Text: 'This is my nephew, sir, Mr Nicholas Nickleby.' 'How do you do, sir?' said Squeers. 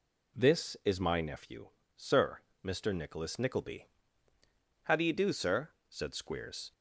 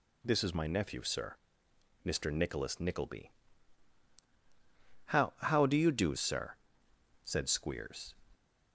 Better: first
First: none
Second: says "How" twice; at 5.3 s

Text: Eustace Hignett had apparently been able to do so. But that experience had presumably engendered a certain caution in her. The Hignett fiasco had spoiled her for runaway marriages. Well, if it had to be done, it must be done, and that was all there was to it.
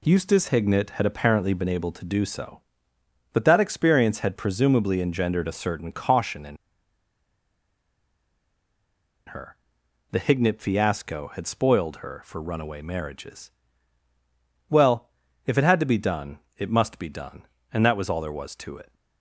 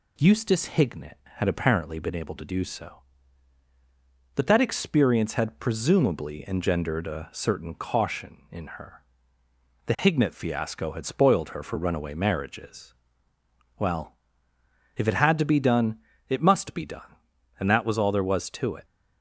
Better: second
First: pauses between "in" and "her"; strong; at 6.5 s; 2.7 s long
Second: none

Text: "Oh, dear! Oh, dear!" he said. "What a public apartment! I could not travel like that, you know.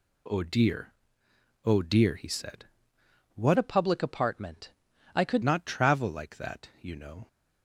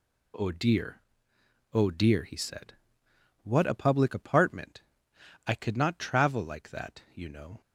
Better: second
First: changes voice from "a" to "could"; from 3.5 to 5.4 s; 1.9 s long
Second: none

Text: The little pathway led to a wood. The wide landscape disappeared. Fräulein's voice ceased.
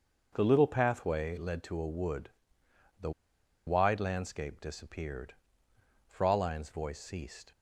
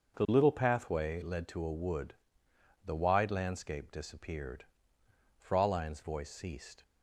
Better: second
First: pauses between "The" and "wide"; noticeable; at 3.1 s; 0.55 s long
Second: none

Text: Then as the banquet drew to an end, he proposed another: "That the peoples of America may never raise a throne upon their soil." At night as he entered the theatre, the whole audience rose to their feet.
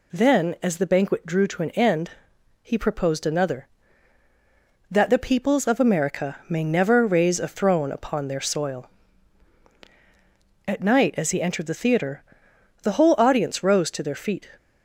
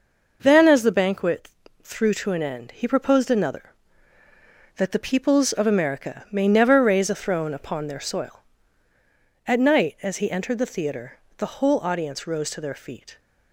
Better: first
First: none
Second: says "threw" for "drew"; at 1.8 s

